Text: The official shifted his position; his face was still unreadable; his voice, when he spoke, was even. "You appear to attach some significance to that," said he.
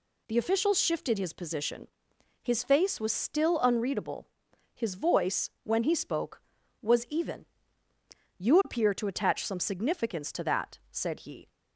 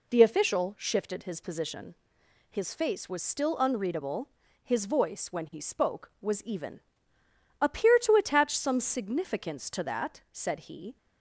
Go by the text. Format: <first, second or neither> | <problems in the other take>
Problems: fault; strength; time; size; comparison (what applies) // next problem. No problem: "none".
first | skips "You"; at 7.2 s